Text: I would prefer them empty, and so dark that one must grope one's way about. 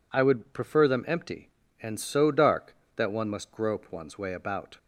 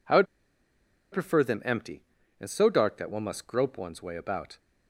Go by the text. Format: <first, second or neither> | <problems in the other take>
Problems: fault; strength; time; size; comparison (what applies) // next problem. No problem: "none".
first | pauses between "would" and "prefer"; noticeable; at 0.2 s; 0.86 s long